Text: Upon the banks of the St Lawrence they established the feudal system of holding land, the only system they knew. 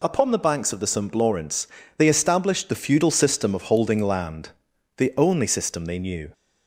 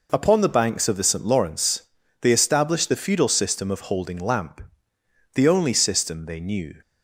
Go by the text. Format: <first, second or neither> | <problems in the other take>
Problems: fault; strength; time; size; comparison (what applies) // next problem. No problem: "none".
first | pauses between "Lawrence" and "they"; at 1.8 s; 0.38 s long; slight in the first // says "lamp" for "land"; at 4.1 s